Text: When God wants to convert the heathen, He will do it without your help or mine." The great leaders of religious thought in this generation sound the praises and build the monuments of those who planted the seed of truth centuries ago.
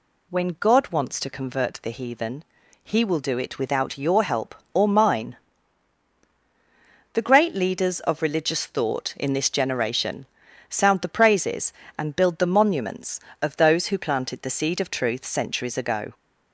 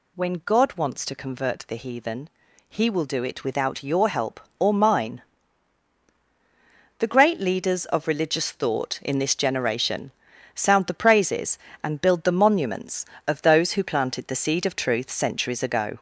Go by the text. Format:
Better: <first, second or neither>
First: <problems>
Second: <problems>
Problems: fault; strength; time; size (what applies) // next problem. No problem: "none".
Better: first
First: pauses between "generation" and "sound"; at 10.2 s; 0.44 s long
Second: gets louder; slight; throughout; 2.5 dB // pauses between "generation" and "sound"; at 10.1 s; 0.44 s long